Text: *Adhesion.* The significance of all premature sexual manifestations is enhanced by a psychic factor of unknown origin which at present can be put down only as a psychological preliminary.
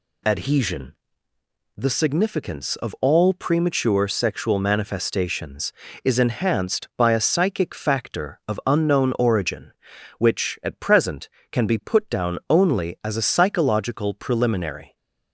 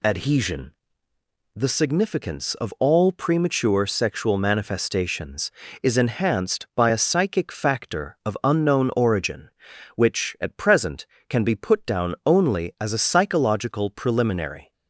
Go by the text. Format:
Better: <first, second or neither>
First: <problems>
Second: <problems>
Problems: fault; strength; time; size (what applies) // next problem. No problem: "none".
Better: neither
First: none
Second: none